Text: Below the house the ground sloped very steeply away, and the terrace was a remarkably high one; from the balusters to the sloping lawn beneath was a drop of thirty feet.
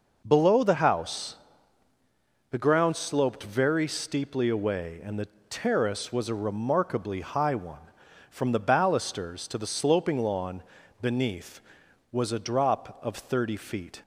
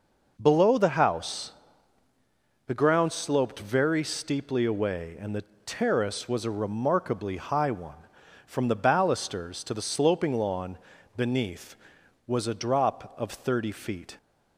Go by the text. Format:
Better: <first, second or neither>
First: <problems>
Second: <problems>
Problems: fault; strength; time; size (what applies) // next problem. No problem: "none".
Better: neither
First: pauses between "house" and "the"; at 1.3 s; 1.1 s long // pauses between "the" and "terrace"; slight; at 5.2 s; 0.22 s long // pauses between "lawn" and "beneath"; slight; at 10.6 s; 0.36 s long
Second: pauses between "house" and "the"; at 1.5 s; 1.1 s long // pauses between "the" and "terrace"; slight; at 5.4 s; 0.22 s long // pauses between "lawn" and "beneath"; slight; at 10.7 s; 0.36 s long